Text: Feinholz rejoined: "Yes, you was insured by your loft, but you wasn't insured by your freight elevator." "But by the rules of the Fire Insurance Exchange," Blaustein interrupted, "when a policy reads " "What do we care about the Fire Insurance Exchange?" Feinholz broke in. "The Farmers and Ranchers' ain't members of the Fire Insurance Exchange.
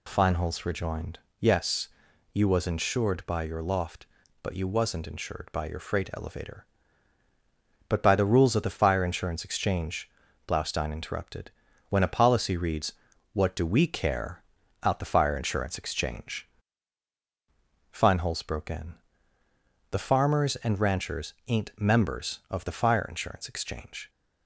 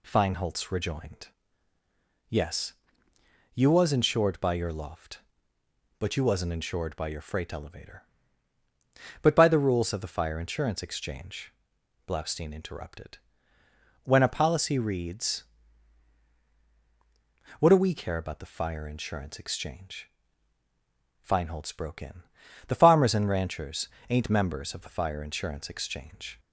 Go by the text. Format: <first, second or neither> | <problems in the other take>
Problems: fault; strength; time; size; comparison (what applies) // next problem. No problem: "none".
second | says "out" for "about"; at 14.8 s // pauses between "Ranchers" and "ain't"; slight; at 21.3 s; 0.16 s long; slight in the second